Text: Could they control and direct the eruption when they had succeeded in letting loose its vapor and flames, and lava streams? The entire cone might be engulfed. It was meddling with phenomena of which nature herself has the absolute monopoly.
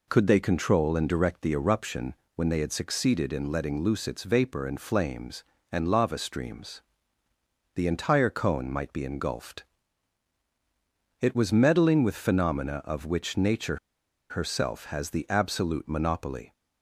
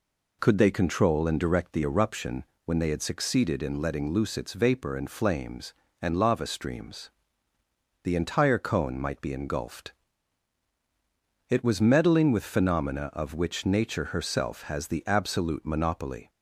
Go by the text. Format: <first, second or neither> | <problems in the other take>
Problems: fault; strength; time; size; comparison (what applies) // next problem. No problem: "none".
second | pauses between "eruption" and "when"; slight; at 2.1 s; 0.20 s long; slight in the second // pauses between "nature" and "herself"; noticeable; at 13.7 s; 0.53 s long